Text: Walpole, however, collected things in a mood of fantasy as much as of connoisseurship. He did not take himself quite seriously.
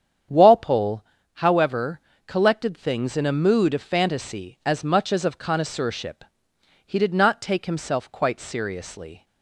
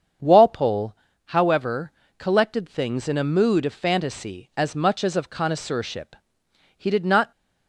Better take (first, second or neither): first